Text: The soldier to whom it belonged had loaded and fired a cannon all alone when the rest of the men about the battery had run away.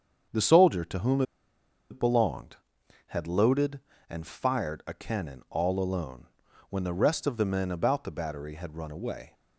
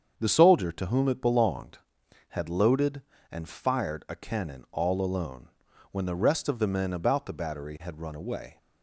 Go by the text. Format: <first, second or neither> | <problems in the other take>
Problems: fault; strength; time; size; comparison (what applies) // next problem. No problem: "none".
second | starts louder than the rest; strong; until 1.9 s; 7.5 dB; strong in the second // pauses between "whom" and "it"; noticeable; at 1.2 s; 0.68 s long // pauses between "alone" and "when"; at 6.2 s; 0.42 s long; also in the second